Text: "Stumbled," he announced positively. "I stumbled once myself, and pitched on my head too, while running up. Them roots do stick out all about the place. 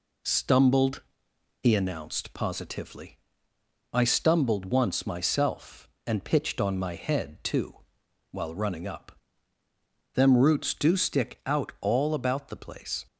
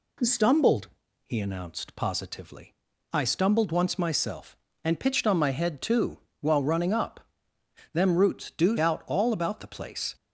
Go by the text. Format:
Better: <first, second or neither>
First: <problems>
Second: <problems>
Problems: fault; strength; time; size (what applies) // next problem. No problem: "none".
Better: first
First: none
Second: skips "stick"; at 8.7 s